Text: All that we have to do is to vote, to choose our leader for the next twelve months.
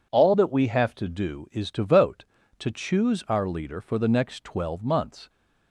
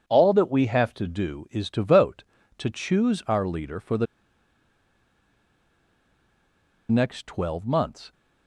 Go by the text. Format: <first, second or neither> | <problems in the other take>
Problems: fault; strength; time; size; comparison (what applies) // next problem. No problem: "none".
first | pauses between "the" and "next"; strong; at 4.0 s; 2.8 s long